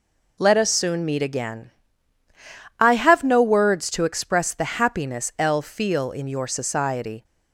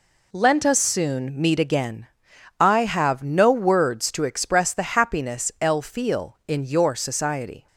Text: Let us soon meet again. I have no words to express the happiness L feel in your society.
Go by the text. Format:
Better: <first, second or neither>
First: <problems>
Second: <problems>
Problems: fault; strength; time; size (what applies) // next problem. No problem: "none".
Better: first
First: none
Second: says "Lent" for "Let"; at 0.3 s